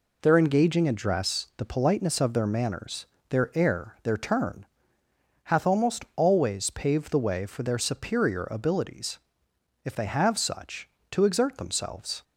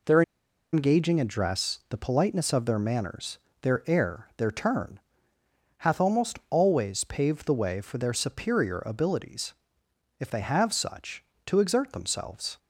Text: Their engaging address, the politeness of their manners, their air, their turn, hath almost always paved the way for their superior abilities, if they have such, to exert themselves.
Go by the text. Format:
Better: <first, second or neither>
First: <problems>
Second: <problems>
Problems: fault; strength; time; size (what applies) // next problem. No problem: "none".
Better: first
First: none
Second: pauses between "Their" and "engaging"; noticeable; at 0.2 s; 0.51 s long